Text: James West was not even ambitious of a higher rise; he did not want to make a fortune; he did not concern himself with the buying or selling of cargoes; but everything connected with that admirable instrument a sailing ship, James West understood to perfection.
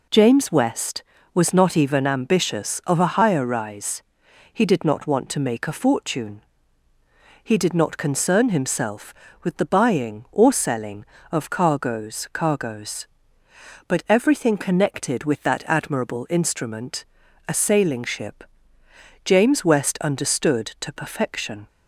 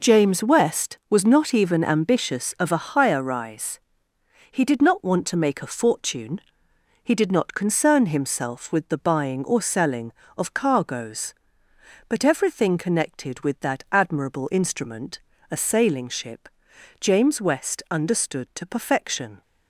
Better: second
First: says "cargoes" twice; at 12.3 s // pauses between "instrument" and "a"; at 17.0 s; 0.42 s long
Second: pauses between "instrument" and "a"; slight; at 15.1 s; 0.32 s long

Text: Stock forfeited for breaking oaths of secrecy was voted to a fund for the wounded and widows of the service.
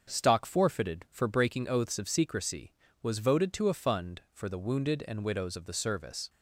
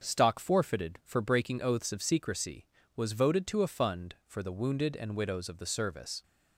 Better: neither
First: starts louder than the rest; until 1.1 s; 7 dB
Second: starts louder than the rest; until 1.0 s; 6.5 dB

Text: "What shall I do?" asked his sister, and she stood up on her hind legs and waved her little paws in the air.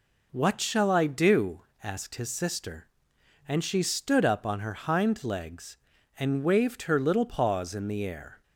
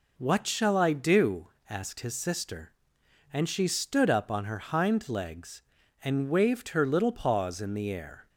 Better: neither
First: none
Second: none

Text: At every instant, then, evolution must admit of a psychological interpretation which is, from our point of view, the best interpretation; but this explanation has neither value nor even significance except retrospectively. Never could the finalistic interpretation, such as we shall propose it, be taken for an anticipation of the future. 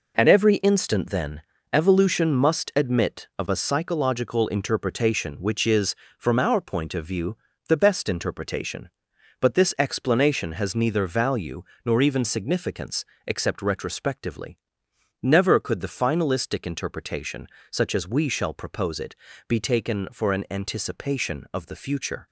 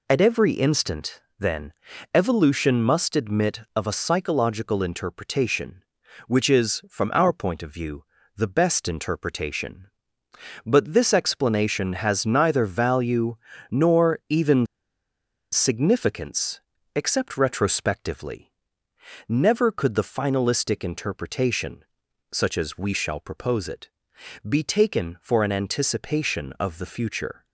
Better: first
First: pauses between "value" and "nor"; slight; at 11.6 s; 0.24 s long // pauses between "significance" and "except"; slight; at 13.0 s; 0.22 s long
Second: pauses between "value" and "nor"; slight; at 13.3 s; 0.36 s long // pauses between "even" and "significance"; noticeable; at 14.6 s; 0.86 s long // pauses between "significance" and "except"; slight; at 16.5 s; 0.34 s long

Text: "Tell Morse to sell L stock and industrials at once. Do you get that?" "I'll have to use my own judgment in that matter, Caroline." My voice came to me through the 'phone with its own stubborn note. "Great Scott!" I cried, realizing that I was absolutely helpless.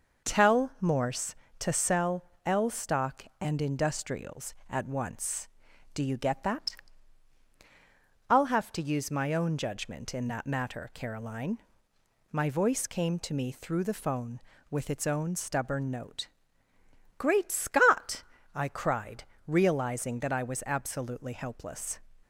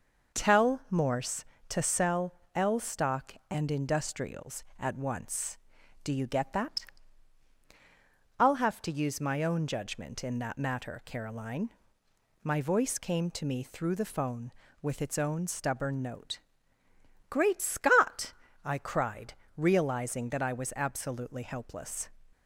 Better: neither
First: pauses between "sell" and "L"; slight; at 2.2 s; 0.20 s long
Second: pauses between "sell" and "L"; slight; at 2.3 s; 0.20 s long

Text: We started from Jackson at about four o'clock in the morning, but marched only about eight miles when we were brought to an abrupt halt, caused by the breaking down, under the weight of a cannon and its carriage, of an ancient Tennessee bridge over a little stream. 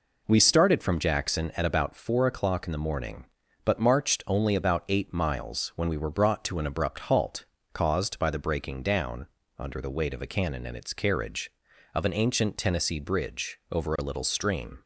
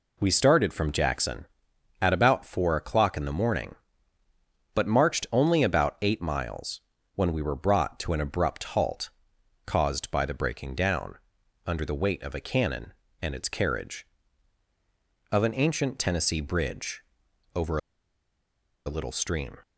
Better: first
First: none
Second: pauses between "miles" and "when"; slight; at 6.8 s; 0.32 s long // pauses between "bridge" and "over"; noticeable; at 17.0 s; 0.50 s long // pauses between "over" and "a"; at 17.7 s; 1.0 s long

